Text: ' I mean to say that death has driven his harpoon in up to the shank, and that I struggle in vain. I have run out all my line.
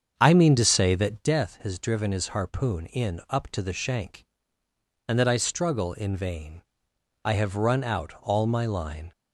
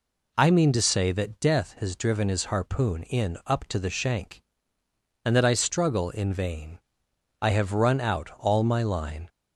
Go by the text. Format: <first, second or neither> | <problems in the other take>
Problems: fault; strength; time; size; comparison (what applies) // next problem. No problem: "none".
second | starts louder than the rest; strong; until 1.3 s; 7 dB